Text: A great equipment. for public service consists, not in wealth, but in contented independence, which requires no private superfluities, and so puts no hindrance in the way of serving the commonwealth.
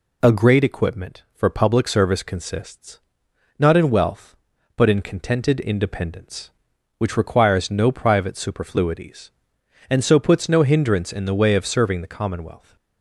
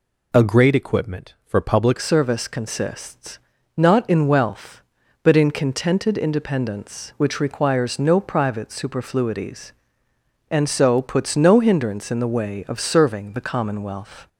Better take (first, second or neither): first